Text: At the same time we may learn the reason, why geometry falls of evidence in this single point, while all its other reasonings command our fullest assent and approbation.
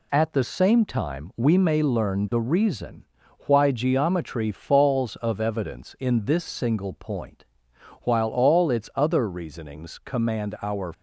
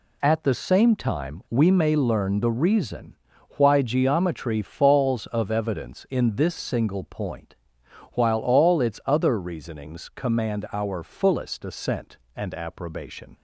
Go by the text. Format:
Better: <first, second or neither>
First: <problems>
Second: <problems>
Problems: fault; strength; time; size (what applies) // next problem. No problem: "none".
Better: second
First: stops before "fullest assent and approbation"; at 10.9 s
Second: none